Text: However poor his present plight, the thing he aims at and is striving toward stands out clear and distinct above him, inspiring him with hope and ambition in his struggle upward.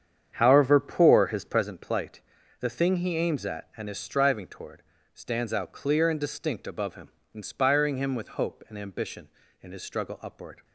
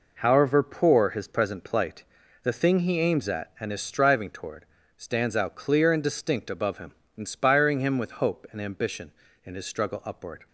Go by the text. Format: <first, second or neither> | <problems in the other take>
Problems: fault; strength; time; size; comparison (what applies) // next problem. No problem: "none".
second | starts louder than the rest; strong; until 1.7 s; 8 dB // pauses between "toward" and "stands"; slight; at 4.8 s; 0.32 s long; slight in the second